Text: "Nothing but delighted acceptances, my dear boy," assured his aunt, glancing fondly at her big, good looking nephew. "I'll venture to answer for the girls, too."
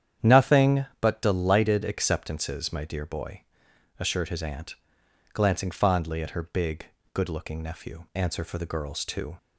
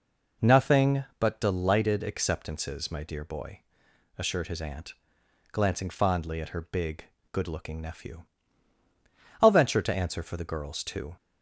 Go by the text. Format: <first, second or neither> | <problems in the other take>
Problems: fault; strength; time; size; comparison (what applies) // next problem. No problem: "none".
second | starts louder than the rest; strong; until 1.3 s; 9 dB // skips "I'll venture to"; at 8.1 s